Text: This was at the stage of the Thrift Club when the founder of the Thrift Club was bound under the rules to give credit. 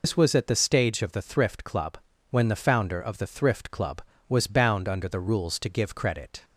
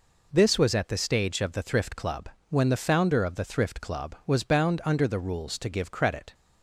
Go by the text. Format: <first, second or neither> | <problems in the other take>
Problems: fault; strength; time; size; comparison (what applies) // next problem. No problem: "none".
second | loses the start of "This"; at 0.0 s; 70 ms // pauses between "Club" and "when"; slight; at 1.9 s; 0.32 s long; slight in the second